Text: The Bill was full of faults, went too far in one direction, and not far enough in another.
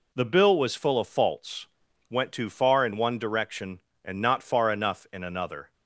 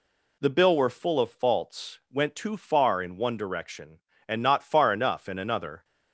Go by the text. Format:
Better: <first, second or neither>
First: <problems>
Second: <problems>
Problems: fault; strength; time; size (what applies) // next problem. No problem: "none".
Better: first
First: none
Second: says "were" for "was"; at 0.7 s